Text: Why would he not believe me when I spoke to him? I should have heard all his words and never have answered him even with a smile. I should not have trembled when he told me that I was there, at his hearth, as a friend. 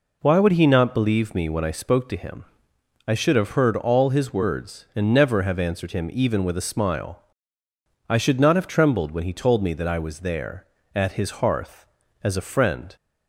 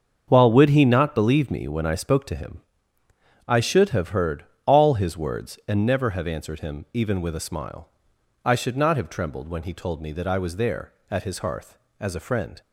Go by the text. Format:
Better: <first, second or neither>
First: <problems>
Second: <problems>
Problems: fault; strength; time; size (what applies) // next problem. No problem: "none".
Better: first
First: none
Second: starts louder than the rest; until 1.2 s; 7 dB // says "While" for "Why"; at 0.2 s // pauses between "heard" and "all"; slight; at 4.4 s; 0.22 s long